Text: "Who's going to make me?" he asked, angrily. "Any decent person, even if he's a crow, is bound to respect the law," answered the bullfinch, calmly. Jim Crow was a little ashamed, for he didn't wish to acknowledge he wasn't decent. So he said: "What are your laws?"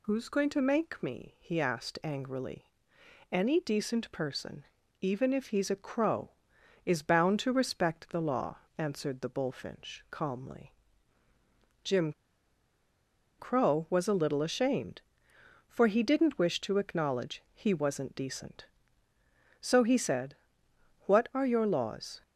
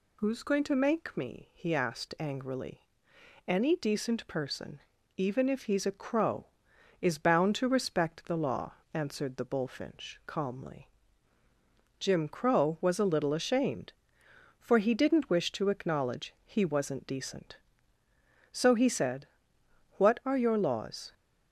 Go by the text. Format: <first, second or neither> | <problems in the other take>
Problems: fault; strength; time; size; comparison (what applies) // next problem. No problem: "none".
second | pauses between "Jim" and "Crow"; strong; at 12.1 s; 1.2 s long